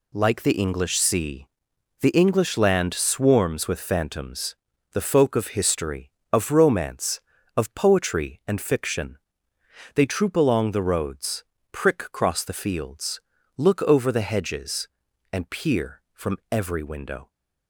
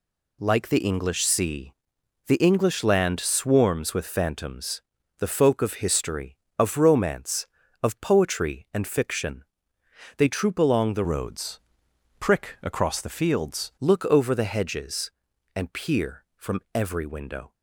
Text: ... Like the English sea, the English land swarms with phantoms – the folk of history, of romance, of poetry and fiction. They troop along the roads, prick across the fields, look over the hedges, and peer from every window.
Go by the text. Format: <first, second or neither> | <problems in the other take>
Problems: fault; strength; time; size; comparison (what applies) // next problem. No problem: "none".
first | changes voice from "roads" to "fields"; from 11.0 to 13.7 s; 2.7 s long